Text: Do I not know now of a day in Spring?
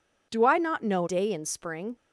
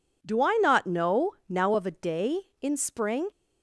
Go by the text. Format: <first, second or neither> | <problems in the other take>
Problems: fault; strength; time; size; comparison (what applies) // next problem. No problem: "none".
second | skips "now of a"; at 1.0 s